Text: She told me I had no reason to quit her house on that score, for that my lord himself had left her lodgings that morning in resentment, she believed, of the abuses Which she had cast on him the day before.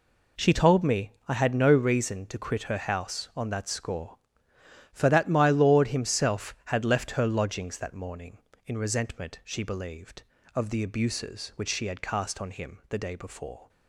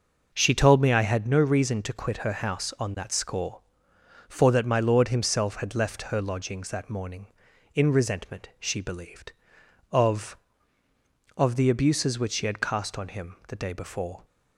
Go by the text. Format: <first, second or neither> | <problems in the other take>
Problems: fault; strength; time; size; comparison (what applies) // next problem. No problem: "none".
first | says "of" twice; at 11.3 s